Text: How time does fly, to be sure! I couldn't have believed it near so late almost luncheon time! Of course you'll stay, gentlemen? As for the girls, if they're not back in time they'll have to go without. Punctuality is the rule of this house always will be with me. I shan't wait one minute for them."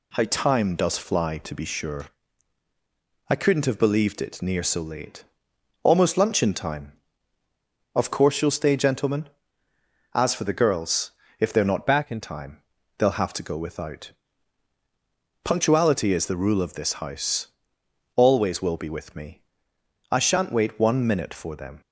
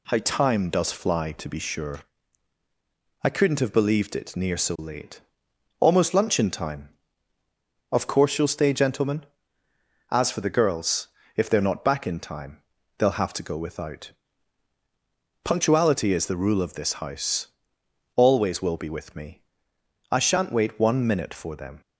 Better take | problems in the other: second | pauses between "late" and "almost"; noticeable; at 5.2 s; 0.60 s long; noticeable in the second // changes voice from "back" to "in"; from 11.8 to 12.1 s; 0.3 s long // pauses between "time" and "they'll"; slight; at 12.6 s; 0.34 s long; slight in the second // pauses between "house" and "always"; noticeable; at 17.4 s; 0.68 s long; noticeable in the second

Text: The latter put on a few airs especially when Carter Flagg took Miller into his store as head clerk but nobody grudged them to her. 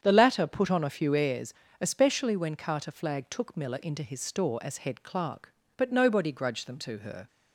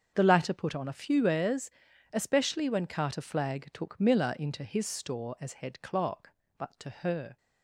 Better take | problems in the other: first | starts louder than the rest; until 1.1 s; 7 dB; strong in the first // pauses between "airs" and "especially"; at 1.7 s; 0.42 s long; slight in the first // skips "nobody grudged them"; at 6.7 s

